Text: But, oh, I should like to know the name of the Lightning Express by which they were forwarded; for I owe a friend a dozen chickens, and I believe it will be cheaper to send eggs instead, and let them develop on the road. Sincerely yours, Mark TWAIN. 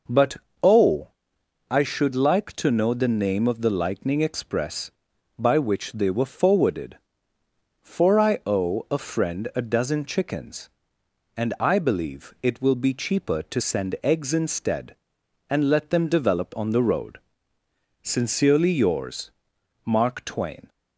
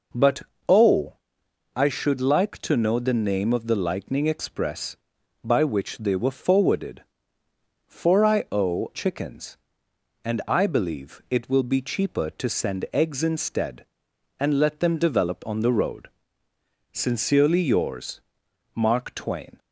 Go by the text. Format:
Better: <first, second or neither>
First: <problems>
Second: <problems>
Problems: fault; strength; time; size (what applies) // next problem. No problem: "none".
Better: first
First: none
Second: skips "a friend a dozen"; at 8.9 s